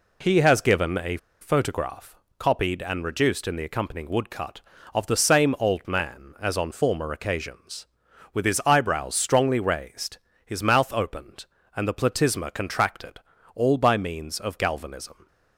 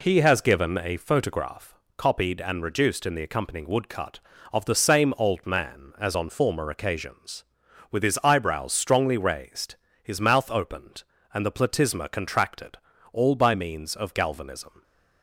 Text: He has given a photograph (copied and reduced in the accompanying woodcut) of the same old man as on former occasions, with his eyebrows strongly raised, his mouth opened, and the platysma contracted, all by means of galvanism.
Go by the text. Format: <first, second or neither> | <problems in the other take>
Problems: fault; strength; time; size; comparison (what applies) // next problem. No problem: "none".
second | pauses between "a" and "photograph"; slight; at 1.1 s; 0.23 s long